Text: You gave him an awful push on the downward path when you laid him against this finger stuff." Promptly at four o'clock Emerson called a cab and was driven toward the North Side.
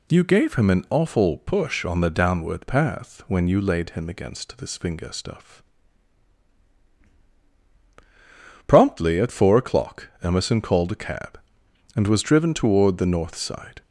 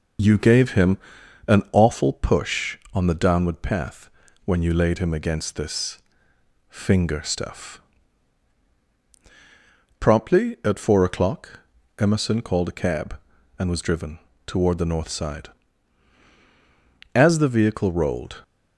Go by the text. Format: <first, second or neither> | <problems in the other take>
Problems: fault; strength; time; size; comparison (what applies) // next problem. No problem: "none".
first | pauses between "him" and "an"; noticeable; at 0.9 s; 0.48 s long // pauses between "path" and "when"; slight; at 4.1 s; 0.34 s long // pauses between "this" and "finger"; noticeable; at 5.9 s; 0.72 s long // pauses between "o'clock" and "Emerson"; slight; at 11.6 s; 0.36 s long; slight in the first // pauses between "driven" and "toward"; slight; at 14.1 s; 0.26 s long // goes on to say "As the vehicle rolled"; noticeable; from 17.1 s on; 1.2 s long